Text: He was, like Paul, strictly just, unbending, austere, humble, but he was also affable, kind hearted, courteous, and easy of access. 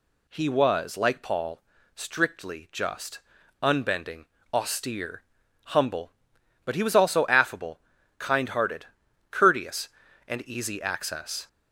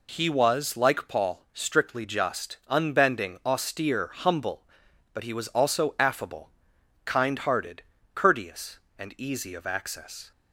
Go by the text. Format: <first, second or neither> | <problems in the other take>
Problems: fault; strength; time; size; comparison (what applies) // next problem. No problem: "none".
second | skips "of"; at 10.8 s